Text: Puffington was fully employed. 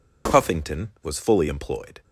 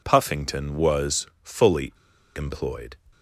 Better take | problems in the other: first | pauses between "was" and "fully"; slight; at 1.2 s; 0.18 s long // pauses between "fully" and "employed"; at 1.9 s; 0.42 s long

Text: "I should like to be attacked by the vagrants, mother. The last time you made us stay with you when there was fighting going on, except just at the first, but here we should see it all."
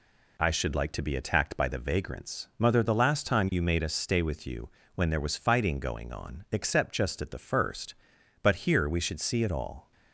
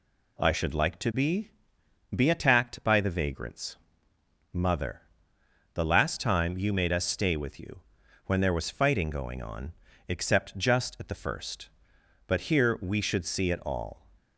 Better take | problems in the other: first | says "be" twice; at 2.1 s // pauses between "you" and "when"; at 7.8 s; 0.44 s long; slight in the first

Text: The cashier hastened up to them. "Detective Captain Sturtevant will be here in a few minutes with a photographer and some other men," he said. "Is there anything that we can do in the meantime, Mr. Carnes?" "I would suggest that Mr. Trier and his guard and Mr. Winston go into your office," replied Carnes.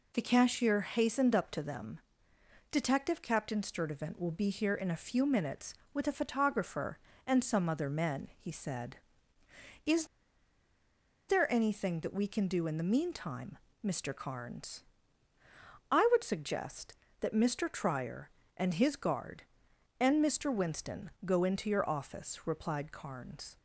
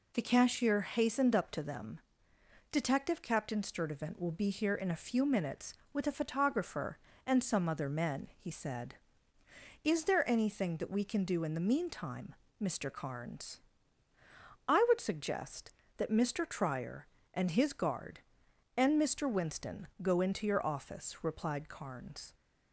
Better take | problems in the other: second | pauses between "Is" and "there"; at 10.0 s; 1.2 s long // pauses between "Winston" and "go"; slight; at 21.0 s; 0.16 s long; slight in the second

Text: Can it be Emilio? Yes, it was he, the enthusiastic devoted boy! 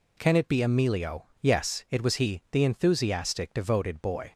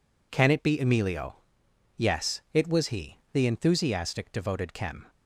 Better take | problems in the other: first | says "kem" for "boy"; at 4.7 s

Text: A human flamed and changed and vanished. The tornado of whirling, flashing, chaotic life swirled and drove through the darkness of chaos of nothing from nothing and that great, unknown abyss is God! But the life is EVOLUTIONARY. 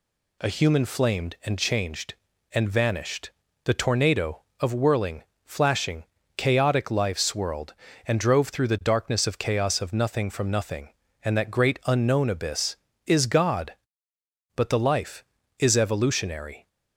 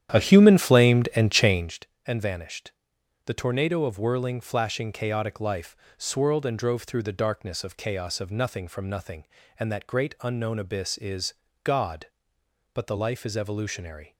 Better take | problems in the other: first | starts louder than the rest; strong; until 1.8 s; 10.5 dB // pauses between "life" and "swirled"; slight; at 5.7 s; 0.21 s long // pauses between "is" and "God"; slight; at 11.3 s; 0.28 s long

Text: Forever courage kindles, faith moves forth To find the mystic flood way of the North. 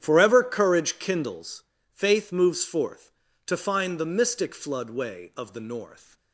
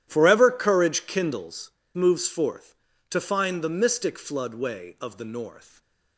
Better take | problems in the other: first | starts louder than the rest; strong; until 1.0 s; 11 dB; strong in the first // skips "faith"; at 1.8 s // stays silent after the last word; slight; from 5.6 s on; 0.5 s long

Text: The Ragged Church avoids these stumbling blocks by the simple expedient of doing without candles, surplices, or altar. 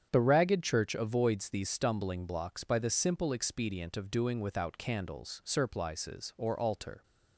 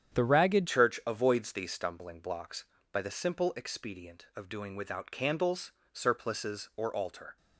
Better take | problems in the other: first | starts louder than the rest; strong; until 1.2 s; 9 dB; strong in the first // changes voice at "Church"; from 0.6 s on; 6.7 s long

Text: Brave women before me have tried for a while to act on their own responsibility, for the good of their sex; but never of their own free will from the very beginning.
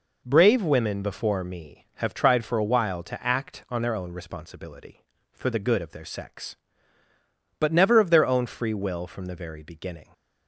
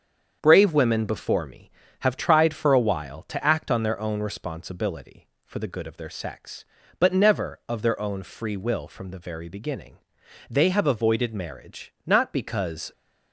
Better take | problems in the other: first | starts louder than the rest; strong; until 1.4 s; 7.5 dB // goes on to say "They have avoided marriage not because"; strong; from 10.4 s on; 2.4 s long

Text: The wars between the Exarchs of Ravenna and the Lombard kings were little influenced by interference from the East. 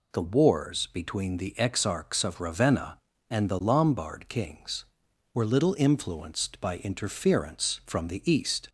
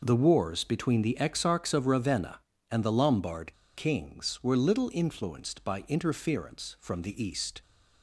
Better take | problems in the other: first | pauses between "Lombard" and "kings"; slight; at 3.5 s; 0.23 s long

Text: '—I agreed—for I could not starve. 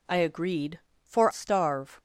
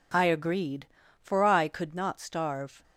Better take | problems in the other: second | skips "I could not"; at 1.3 s

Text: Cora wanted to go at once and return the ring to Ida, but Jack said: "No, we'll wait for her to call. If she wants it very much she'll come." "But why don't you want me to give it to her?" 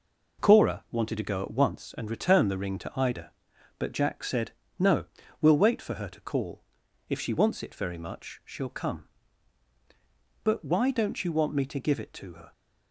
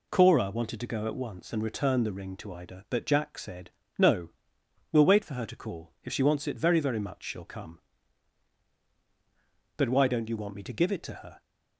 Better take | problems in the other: first | says "very" twice; at 6.7 s

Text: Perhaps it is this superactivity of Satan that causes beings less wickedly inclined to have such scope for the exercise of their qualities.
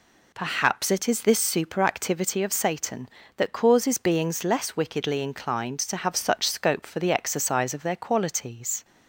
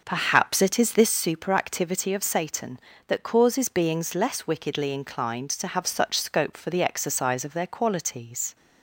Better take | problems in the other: first | starts louder than the rest; noticeable; until 1.1 s; 5.5 dB

